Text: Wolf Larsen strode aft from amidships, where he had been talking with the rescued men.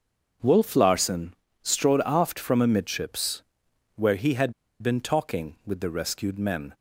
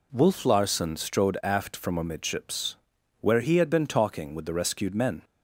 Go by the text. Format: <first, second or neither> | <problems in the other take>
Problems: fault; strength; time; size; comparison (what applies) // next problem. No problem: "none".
second | starts louder than the rest; until 1.7 s; 6.5 dB // pauses between "Larsen" and "strode"; slight; at 1.3 s; 0.28 s long // pauses between "had" and "been"; slight; at 4.5 s; 0.30 s long